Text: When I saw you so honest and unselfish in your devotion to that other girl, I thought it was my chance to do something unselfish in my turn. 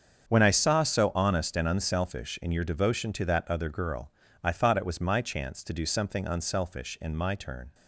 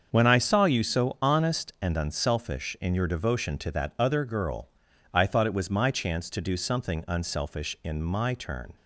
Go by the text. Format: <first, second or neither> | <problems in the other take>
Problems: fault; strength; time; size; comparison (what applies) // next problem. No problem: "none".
second | starts louder than the rest; strong; until 1.3 s; 7 dB; also in the second // skips "you"; at 0.8 s